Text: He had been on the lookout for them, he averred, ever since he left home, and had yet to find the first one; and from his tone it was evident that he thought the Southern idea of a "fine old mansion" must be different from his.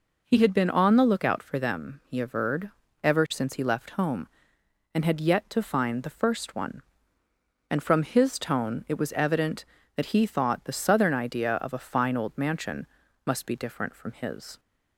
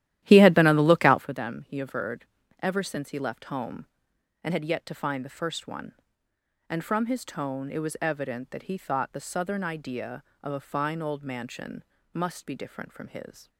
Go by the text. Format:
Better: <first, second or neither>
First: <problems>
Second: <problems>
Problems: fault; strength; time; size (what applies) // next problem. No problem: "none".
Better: first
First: pauses between "mansion" and "must"; at 12.8 s; 0.40 s long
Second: starts louder than the rest; strong; until 1.3 s; 13 dB // pauses between "mansion" and "must"; slight; at 11.8 s; 0.30 s long